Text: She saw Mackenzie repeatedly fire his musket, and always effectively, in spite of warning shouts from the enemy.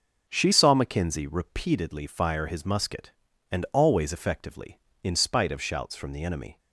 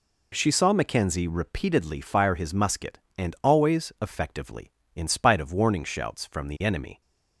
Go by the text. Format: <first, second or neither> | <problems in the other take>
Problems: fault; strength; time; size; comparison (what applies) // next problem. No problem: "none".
second | skips "warning"; at 5.6 s